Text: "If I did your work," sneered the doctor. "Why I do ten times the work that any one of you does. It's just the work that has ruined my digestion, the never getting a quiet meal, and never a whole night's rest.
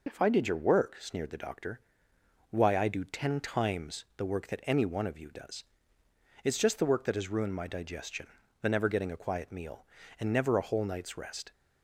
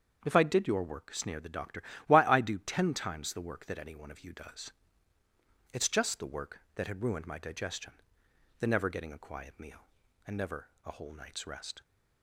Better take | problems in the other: first | starts louder than the rest; until 1.2 s; 7 dB // says "had" for "has"; at 6.8 s // pauses between "never" and "a"; slight; at 10.6 s; 0.16 s long

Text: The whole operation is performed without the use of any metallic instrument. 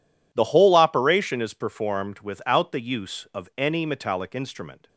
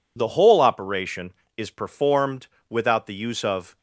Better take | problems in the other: first | pauses between "performed" and "without"; slight; at 2.4 s; 0.24 s long // stops before "any metallic instrument"; at 3.7 s

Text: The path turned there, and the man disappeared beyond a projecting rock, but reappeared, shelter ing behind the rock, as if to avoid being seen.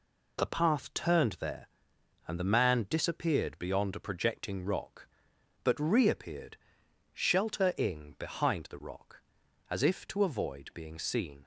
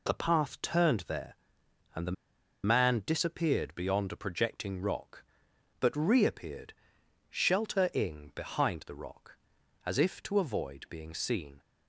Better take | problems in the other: first | pauses between "the" and "man"; noticeable; at 2.1 s; 0.51 s long

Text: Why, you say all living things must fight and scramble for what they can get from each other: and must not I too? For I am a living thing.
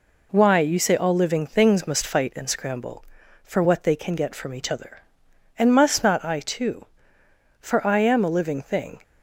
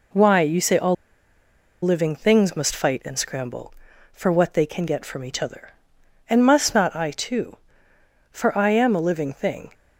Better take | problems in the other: first | pauses between "all" and "living"; noticeable; at 0.9 s; 0.89 s long

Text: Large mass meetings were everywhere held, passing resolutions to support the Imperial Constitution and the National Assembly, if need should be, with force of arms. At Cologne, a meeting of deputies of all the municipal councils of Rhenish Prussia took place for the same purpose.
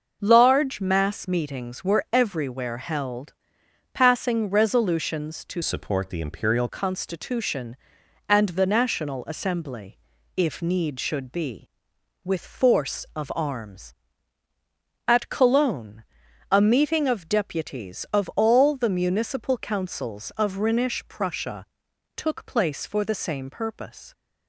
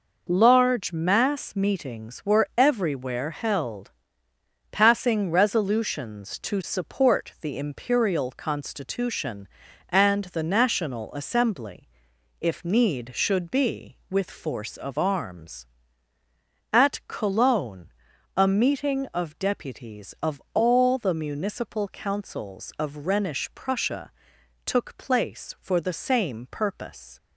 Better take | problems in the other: second | changes voice from "support" to "Imperial"; from 5.6 to 6.6 s; 1.0 s long // pauses between "Prussia" and "took"; noticeable; at 21.6 s; 0.50 s long; noticeable in the second

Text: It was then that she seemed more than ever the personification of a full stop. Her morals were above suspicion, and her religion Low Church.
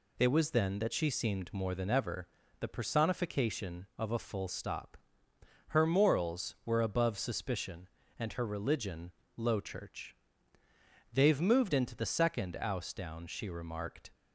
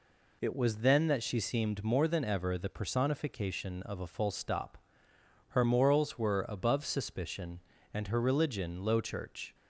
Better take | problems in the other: second | pauses between "ever" and "the"; slight; at 2.2 s; 0.34 s long // pauses between "religion" and "Low"; slight; at 9.1 s; 0.24 s long // goes on to say "They've moved into the second ouse down she remarked"; strong; from 11.1 s on; 3.0 s long

